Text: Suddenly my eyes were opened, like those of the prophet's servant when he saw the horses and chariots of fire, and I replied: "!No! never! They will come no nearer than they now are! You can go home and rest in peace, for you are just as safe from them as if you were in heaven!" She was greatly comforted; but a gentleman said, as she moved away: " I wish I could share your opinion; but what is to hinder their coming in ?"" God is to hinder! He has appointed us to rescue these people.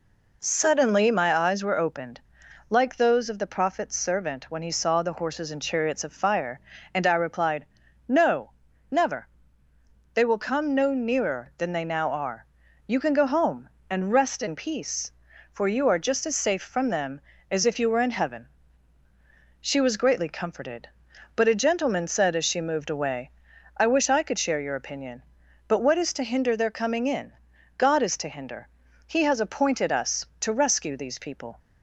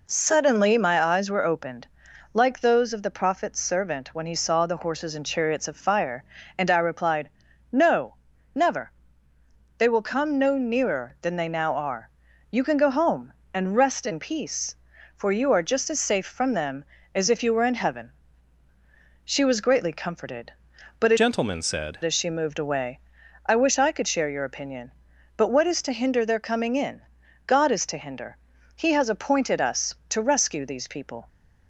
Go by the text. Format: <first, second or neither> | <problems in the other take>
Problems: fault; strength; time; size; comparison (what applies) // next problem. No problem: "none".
first | changes voice from "gentleman" to "said"; from 21.1 to 21.9 s; 0.8 s long